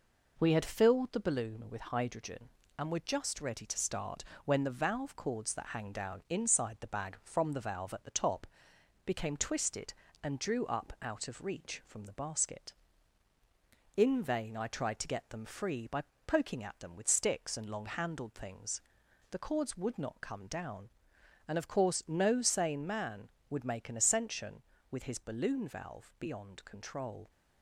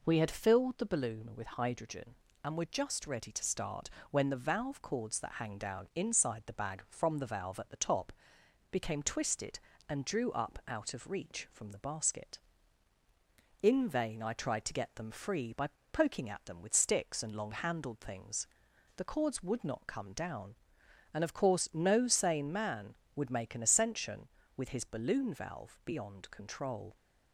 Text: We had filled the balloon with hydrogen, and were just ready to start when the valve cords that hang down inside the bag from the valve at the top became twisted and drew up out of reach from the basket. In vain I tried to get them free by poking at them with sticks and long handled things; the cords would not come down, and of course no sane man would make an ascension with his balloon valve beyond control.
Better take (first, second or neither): second